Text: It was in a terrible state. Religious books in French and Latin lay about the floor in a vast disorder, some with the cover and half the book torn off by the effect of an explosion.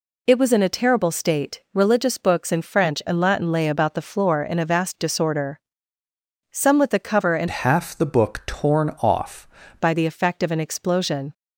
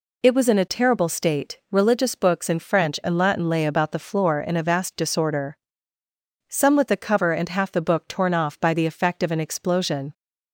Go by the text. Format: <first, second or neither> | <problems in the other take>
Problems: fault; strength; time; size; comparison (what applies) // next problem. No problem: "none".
second | changes voice from "half" to "off"; from 7.4 to 9.4 s; 2.0 s long